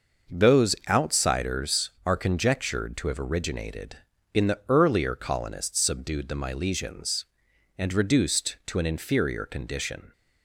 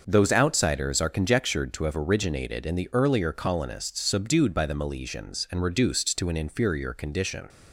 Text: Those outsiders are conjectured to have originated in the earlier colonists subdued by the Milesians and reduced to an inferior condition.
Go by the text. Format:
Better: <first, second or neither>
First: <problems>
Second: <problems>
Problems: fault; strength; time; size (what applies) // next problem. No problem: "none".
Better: second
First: starts louder than the rest; noticeable; until 1.4 s; 6 dB // skips "by"; at 6.2 s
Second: starts louder than the rest; until 1.0 s; 6 dB